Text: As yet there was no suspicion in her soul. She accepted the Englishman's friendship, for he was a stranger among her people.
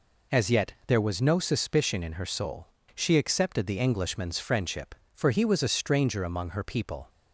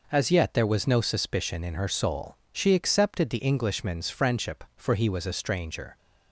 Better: first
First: none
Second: stops before "among her people"; at 5.9 s

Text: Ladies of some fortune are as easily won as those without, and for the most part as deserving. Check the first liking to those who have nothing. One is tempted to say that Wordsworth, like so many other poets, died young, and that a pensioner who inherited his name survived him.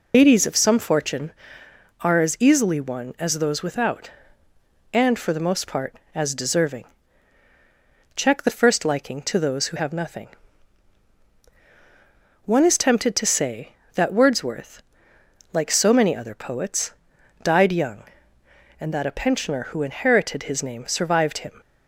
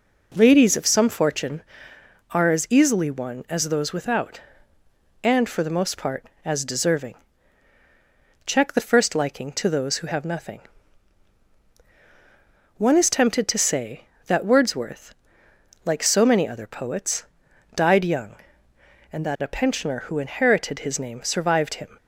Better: second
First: loses the start of "Ladies"; at 0.1 s; 130 ms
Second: none

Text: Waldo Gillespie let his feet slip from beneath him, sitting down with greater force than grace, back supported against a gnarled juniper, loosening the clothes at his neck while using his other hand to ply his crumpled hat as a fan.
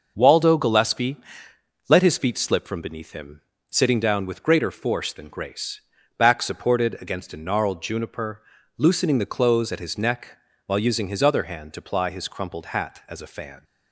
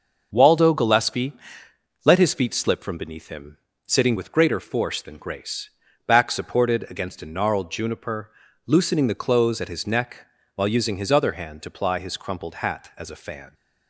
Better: first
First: pauses between "Gillespie" and "let"; noticeable; at 1.1 s; 0.72 s long // pauses between "neck" and "while"; slight; at 10.3 s; 0.30 s long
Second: pauses between "Gillespie" and "let"; noticeable; at 1.3 s; 0.72 s long // skips "down"; at 4.1 s // pauses between "neck" and "while"; slight; at 10.2 s; 0.30 s long

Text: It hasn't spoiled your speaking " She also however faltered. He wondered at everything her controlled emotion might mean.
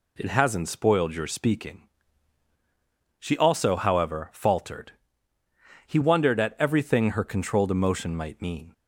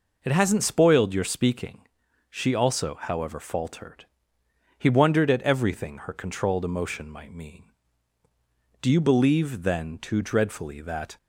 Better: first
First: none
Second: goes on to say "Do you believe then too dreadfully that"; strong; from 8.8 s on; 2.3 s long

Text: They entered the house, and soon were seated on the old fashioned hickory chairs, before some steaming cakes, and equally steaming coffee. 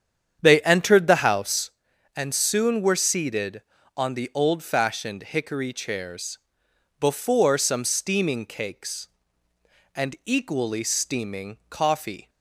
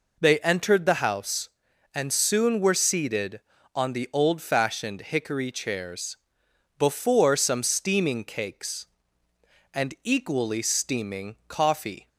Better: second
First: starts louder than the rest; strong; until 1.8 s; 8.5 dB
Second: none

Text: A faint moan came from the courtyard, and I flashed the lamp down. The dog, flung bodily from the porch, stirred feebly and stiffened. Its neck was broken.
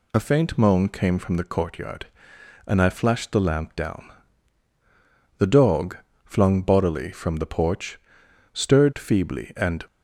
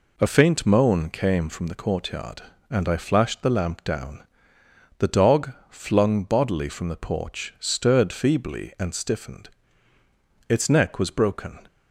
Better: second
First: stops before "stiffened Its neck was broken"; at 9.8 s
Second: none

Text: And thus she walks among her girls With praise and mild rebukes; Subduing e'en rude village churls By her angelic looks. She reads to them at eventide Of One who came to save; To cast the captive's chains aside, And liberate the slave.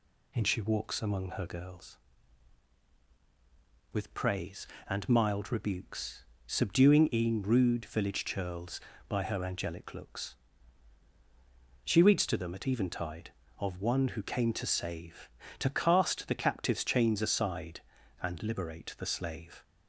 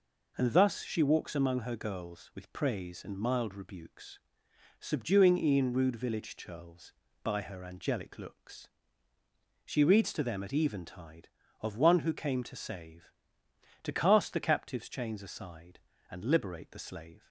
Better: second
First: skips "thus"; at 0.4 s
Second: none

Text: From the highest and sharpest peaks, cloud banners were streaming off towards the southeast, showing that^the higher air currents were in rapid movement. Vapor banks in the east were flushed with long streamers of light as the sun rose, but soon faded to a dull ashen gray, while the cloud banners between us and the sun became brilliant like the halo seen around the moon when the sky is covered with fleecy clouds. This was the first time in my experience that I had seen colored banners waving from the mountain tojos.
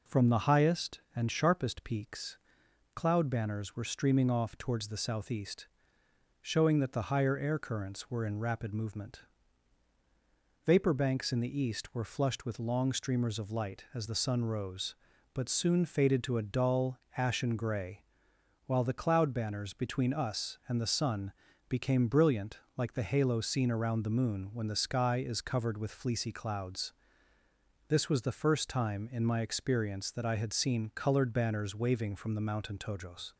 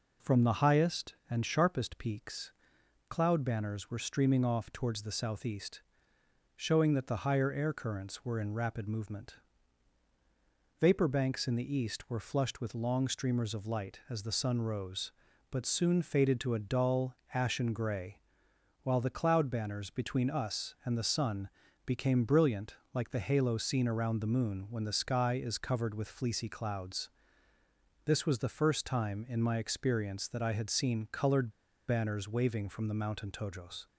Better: first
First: pauses between "dull" and "ashen"; slight; at 16.9 s; 0.18 s long // pauses between "sun" and "became"; at 21.3 s; 0.38 s long // pauses between "brilliant" and "like"; slight; at 22.5 s; 0.18 s long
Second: pauses between "dull" and "ashen"; slight; at 17.1 s; 0.18 s long // pauses between "sun" and "became"; at 21.4 s; 0.38 s long // pauses between "brilliant" and "like"; slight; at 22.7 s; 0.18 s long // pauses between "colored" and "banners"; at 31.5 s; 0.37 s long

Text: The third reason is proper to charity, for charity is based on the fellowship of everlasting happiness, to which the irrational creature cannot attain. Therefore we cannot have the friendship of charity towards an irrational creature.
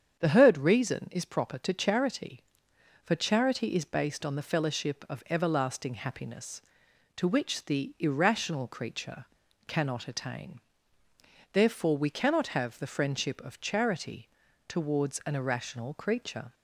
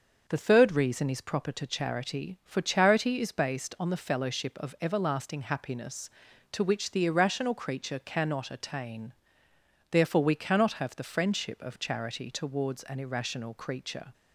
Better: second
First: starts louder than the rest; strong; until 1.2 s; 8 dB // says "heard" for "third"; at 0.2 s // pauses between "creature" and "cannot"; at 9.2 s; 0.42 s long // pauses between "charity" and "towards"; at 14.2 s; 0.40 s long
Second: starts louder than the rest; until 1.2 s; 6 dB

